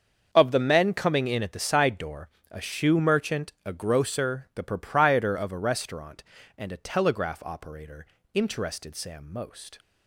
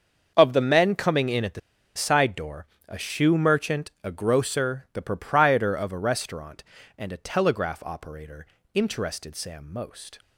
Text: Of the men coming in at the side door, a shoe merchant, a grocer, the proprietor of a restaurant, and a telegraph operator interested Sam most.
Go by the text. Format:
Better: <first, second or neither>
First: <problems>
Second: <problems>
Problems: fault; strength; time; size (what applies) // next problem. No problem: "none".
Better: first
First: starts louder than the rest; until 1.3 s; 6.5 dB // pauses between "operator" and "interested"; slight; at 8.0 s; 0.30 s long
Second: starts louder than the rest; until 1.3 s; 6.5 dB // pauses between "the" and "side"; at 1.5 s; 0.36 s long // pauses between "operator" and "interested"; slight; at 8.4 s; 0.30 s long